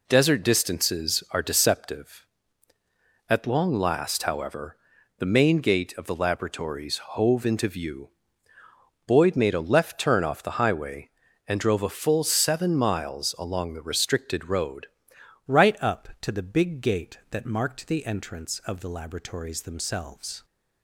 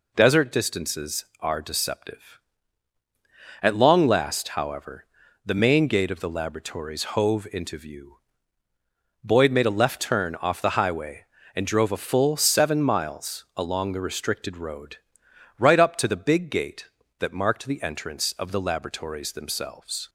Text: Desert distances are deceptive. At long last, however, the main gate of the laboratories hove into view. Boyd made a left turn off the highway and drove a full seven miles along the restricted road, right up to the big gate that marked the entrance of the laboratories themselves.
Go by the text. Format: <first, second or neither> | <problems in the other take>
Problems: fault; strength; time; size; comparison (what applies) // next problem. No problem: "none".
second | changes voice at "right"; from 15.4 s on; 5.0 s long